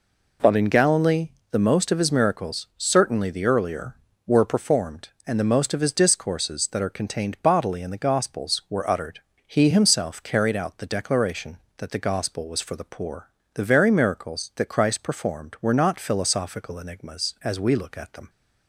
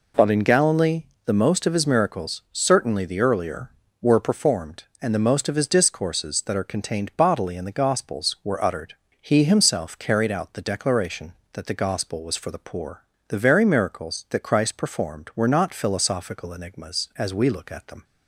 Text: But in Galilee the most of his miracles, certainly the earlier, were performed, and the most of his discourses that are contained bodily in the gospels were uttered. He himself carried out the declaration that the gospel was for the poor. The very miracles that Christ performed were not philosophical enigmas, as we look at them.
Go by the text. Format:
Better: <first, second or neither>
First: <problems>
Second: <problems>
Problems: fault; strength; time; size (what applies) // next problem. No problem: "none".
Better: neither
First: pauses between "Galilee" and "the"; slight; at 1.2 s; 0.22 s long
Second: pauses between "Galilee" and "the"; slight; at 1.0 s; 0.22 s long